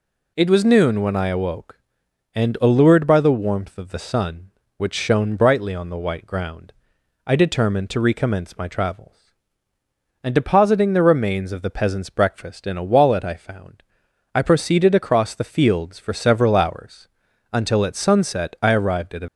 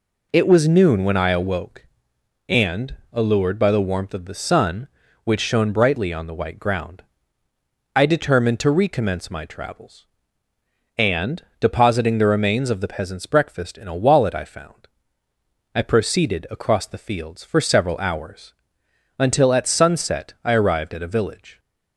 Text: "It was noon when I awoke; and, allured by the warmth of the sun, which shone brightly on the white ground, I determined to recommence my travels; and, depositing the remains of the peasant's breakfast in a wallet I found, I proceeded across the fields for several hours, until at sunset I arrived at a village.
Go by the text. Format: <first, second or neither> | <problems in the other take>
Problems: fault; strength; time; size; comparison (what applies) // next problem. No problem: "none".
second | stops before "village"; at 19.2 s